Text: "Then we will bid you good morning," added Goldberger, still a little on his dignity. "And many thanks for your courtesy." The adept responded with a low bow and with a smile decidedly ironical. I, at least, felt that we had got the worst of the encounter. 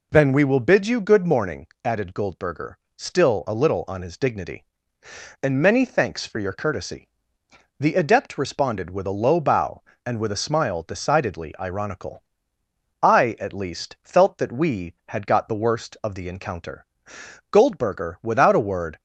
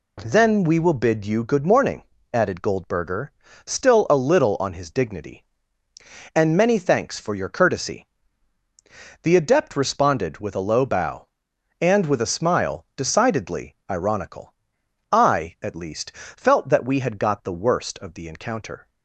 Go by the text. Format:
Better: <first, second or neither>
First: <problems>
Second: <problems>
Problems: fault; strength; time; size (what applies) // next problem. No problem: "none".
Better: second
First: goes on to say "Goldberger without a word"; from 17.4 s on; 1.5 s long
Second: none